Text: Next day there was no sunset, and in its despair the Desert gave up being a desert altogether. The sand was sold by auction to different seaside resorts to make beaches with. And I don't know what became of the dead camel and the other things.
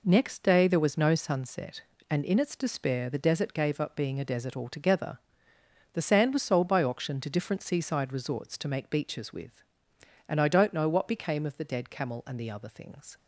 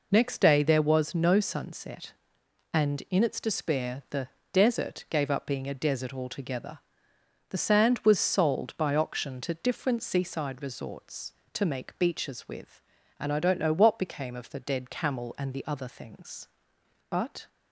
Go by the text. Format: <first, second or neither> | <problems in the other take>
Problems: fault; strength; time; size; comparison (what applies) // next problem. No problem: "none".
first | pauses between "the" and "Desert"; slight; at 4.2 s; 0.24 s long // goes on to say "But"; slight; from 17.0 s on; 0.38 s long